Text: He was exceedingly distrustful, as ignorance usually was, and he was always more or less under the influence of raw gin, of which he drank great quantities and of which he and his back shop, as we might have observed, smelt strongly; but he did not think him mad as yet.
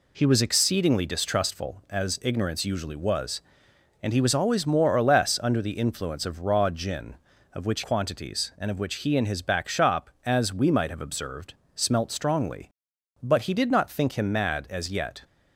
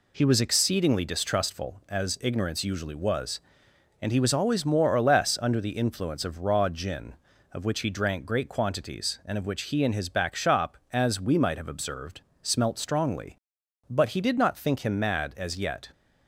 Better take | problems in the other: second | skips "he drank great"; at 7.8 s

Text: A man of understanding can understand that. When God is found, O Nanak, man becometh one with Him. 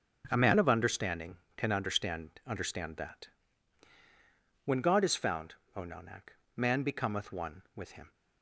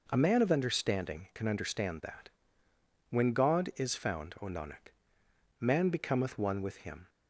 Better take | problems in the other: second | starts louder than the rest; noticeable; until 1.2 s; 6 dB // says "understand" twice; at 2.4 s

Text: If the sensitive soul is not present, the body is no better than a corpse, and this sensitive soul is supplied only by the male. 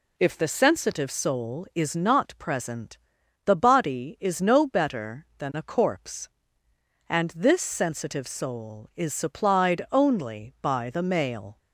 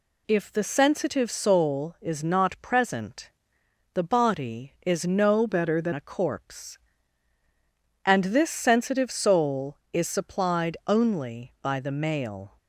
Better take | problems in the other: first | changes voice from "better" to "than"; from 5.4 to 5.9 s; 0.5 s long

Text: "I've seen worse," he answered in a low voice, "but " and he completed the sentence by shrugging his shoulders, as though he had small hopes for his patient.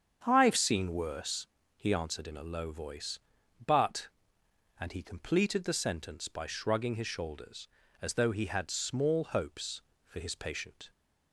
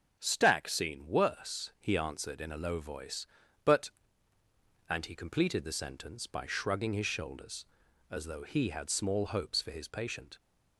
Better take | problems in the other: first | starts louder than the rest; until 1.2 s; 6.5 dB; strong in the first // says "Stack" for "I've"; at 0.1 s

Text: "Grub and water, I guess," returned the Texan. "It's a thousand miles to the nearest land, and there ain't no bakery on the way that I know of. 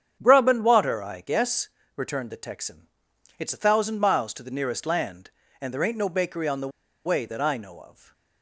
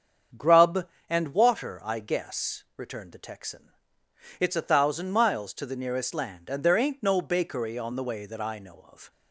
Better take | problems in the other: second | starts louder than the rest; strong; until 1.2 s; 8 dB; strong in the second // pauses between "the" and "way"; at 6.7 s; 0.37 s long // stays silent after the last word; slight; from 7.9 s on; 0.5 s long

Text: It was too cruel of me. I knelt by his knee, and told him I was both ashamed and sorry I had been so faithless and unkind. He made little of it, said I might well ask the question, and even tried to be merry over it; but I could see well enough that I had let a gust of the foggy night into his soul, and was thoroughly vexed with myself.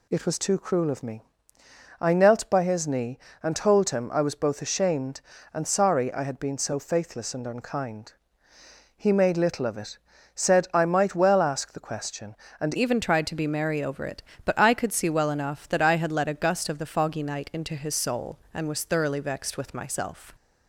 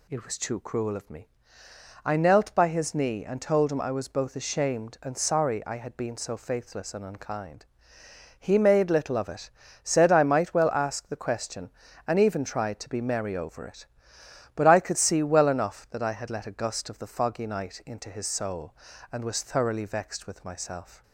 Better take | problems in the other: second | changes voice at "even"; from 12.7 s on; 7.6 s long

